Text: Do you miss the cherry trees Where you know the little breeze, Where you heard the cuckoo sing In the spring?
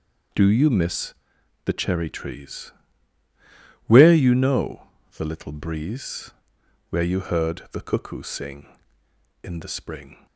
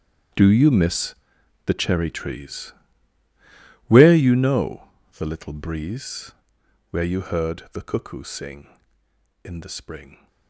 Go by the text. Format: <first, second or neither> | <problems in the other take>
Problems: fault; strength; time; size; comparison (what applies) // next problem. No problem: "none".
first | gets quieter; strong; throughout; 17 dB // pauses between "miss" and "the"; noticeable; at 1.1 s; 0.52 s long; noticeable in the first // pauses between "trees" and "Where"; at 2.7 s; 1.1 s long; also in the first // pauses between "know" and "the"; slight; at 4.8 s; 0.30 s long; slight in the first